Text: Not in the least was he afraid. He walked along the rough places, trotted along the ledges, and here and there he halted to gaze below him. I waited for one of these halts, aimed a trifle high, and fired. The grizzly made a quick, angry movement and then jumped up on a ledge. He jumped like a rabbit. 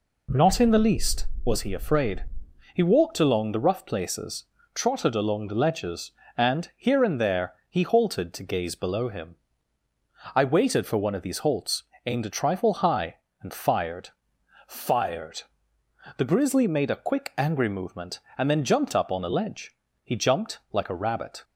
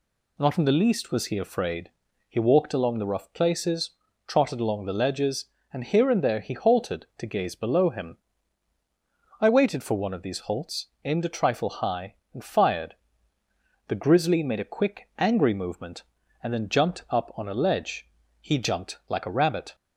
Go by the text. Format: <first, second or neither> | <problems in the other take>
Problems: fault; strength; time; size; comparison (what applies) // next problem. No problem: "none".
second | says "fired" twice; at 14.6 s